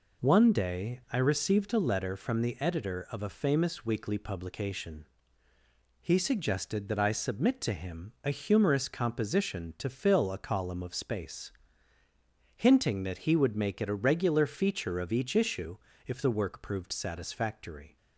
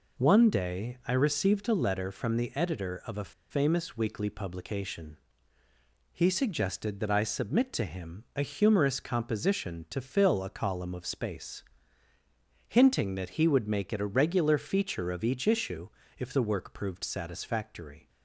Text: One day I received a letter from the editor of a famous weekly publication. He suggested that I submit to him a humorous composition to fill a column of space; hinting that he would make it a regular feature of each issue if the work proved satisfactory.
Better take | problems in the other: first | pauses between "a" and "famous"; slight; at 3.3 s; 0.18 s long // pauses between "issue" and "if"; slight; at 15.8 s; 0.28 s long; slight in the first

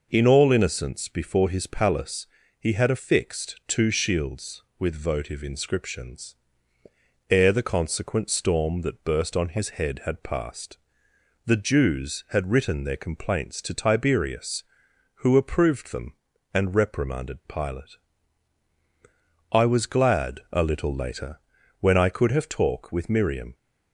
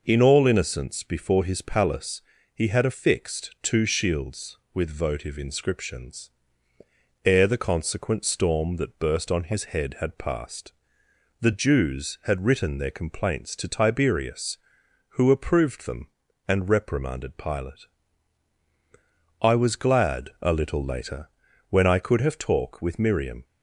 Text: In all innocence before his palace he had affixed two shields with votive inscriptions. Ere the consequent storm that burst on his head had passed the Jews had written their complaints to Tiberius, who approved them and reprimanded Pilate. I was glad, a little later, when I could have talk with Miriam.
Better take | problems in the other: neither | pauses between "palace" and "he"; slight; the same in both // pauses between "passed" and "the"; noticeable; the same in both

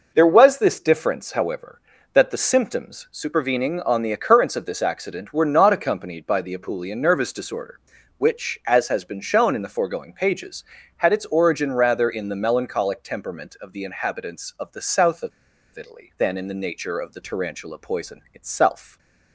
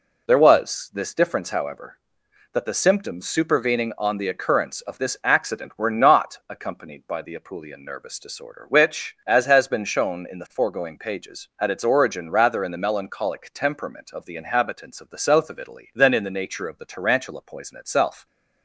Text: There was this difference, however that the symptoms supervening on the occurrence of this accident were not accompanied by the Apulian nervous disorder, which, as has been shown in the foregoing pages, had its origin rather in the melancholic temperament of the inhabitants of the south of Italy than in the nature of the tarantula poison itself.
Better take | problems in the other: second | pauses between "of" and "Italy"; at 15.3 s; 0.44 s long // stays silent after the last word; slight; from 18.8 s on; 0.5 s long

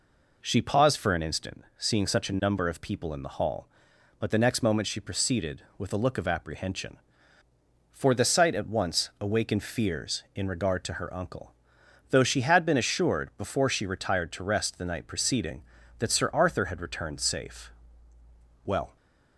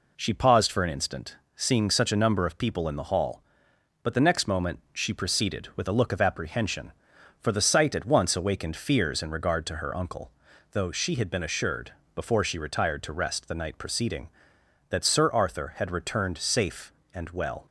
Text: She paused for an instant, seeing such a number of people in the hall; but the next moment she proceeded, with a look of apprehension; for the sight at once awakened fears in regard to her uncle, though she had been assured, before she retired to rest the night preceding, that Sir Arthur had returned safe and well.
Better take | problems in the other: second | skips "and"; at 18.1 s

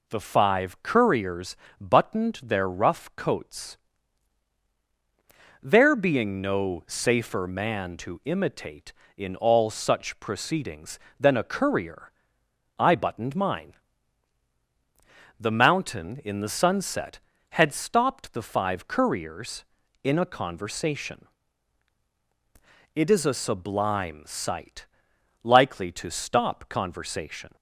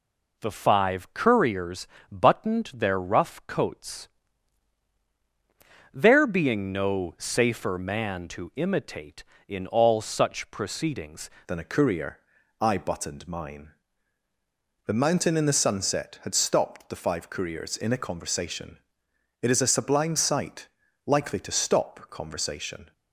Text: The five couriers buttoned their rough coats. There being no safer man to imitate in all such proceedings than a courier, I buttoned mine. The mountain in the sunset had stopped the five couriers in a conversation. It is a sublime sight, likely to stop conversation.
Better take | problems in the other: first | pauses between "couriers" and "buttoned"; slight; at 1.8 s; 0.24 s long; slight in the first // changes voice at "than"; from 11.4 s on; 11.5 s long

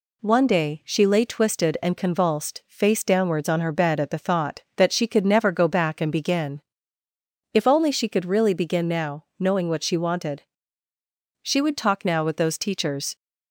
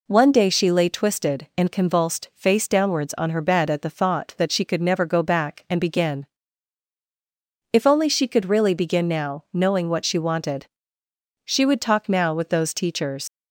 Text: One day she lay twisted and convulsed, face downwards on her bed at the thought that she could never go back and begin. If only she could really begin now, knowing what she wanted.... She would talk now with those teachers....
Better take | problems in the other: first | leaves "teachers" unfinished; at 13.2 s; 100 ms

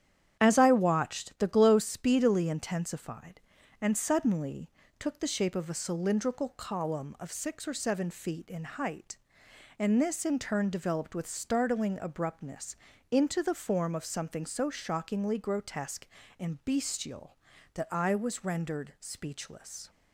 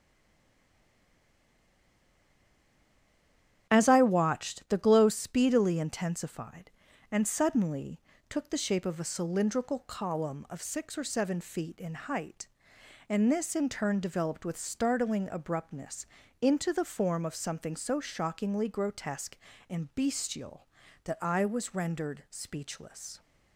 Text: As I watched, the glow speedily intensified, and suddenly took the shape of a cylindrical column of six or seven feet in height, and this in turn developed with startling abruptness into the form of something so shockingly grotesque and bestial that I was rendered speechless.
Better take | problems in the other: first | stays silent before the first word; strong; until 3.6 s; 3.6 s long // starts louder than the rest; strong; until 4.7 s; 9.5 dB; strong in the first // pauses between "suddenly" and "took"; slight; at 7.9 s; 0.32 s long; slight in the first // pauses between "abruptness" and "into"; slight; at 16.0 s; 0.34 s long; slight in the first

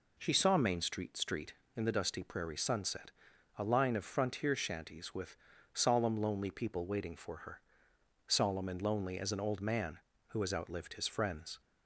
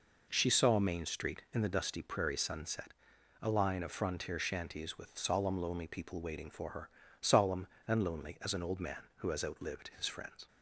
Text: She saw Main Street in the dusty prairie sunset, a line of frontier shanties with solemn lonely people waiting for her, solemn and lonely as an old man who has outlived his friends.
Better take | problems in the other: second | says "Street" twice; at 1.1 s // pauses between "with" and "solemn"; slight; at 5.3 s; 0.36 s long

